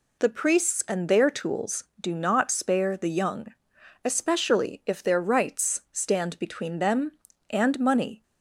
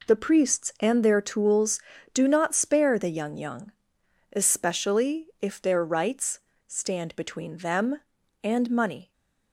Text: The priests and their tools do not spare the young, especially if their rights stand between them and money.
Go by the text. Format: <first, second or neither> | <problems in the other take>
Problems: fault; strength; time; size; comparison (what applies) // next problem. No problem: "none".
first | says "young" twice; at 3.3 s // pauses between "rights" and "stand"; slight; at 6.4 s; 0.26 s long